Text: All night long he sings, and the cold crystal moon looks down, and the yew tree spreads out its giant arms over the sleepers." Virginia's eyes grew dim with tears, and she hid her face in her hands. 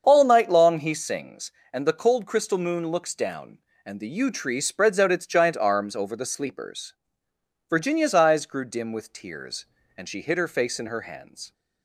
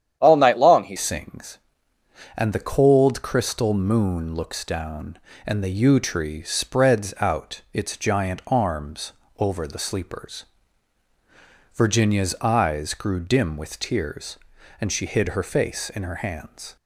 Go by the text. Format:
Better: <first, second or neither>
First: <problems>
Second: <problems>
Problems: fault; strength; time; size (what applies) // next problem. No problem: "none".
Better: first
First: starts louder than the rest; until 1.0 s; 7 dB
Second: starts louder than the rest; strong; until 1.2 s; 10 dB // changes voice at "sings"; from 0.9 s on; 15.8 s long // pauses between "arms" and "over"; slight; at 9.1 s; 0.26 s long